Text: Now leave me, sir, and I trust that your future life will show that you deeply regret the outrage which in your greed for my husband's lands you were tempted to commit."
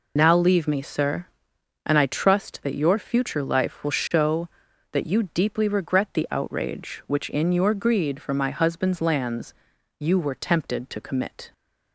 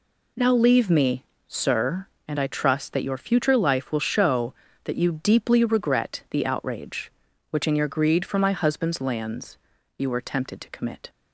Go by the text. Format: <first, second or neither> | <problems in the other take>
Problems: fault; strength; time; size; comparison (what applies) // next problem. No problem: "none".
second | loses the start of "Now"; at 0.1 s; 45 ms // pauses between "lands" and "you"; at 9.5 s; 0.44 s long; also in the second